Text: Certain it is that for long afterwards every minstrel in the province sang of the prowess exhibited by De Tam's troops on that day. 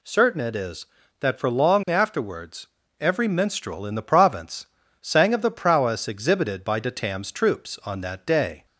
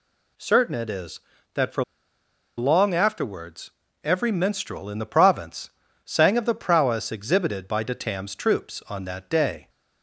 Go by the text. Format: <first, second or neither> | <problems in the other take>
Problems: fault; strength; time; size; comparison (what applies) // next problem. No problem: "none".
first | pauses between "for" and "long"; noticeable; at 1.8 s; 0.74 s long // pauses between "afterwards" and "every"; slight; at 3.7 s; 0.32 s long; slight in the first // pauses between "province" and "sang"; slight; at 5.7 s; 0.34 s long; slight in the first